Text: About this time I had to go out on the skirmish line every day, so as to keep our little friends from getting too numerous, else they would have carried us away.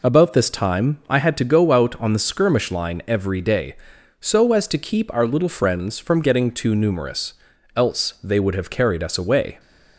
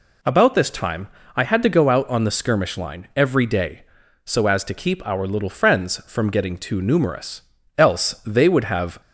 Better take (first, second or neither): first